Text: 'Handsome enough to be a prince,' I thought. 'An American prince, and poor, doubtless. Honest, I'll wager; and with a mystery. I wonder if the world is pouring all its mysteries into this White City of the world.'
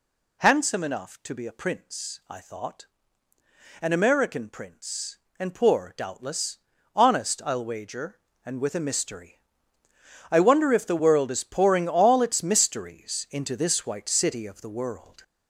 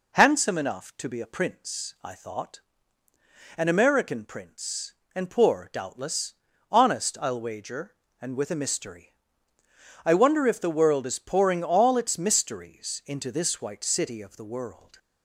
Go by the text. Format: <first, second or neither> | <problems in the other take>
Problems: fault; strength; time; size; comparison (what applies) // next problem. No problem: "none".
second | gets louder; noticeable; throughout; 4 dB